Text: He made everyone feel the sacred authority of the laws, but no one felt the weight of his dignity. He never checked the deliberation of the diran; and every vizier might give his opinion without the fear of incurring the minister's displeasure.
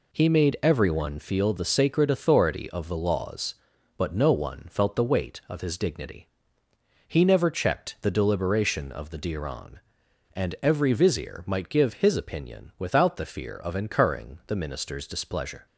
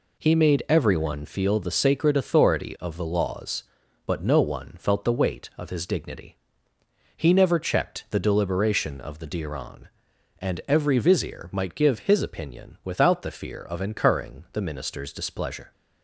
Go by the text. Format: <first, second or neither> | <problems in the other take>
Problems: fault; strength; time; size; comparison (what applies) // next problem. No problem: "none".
neither | none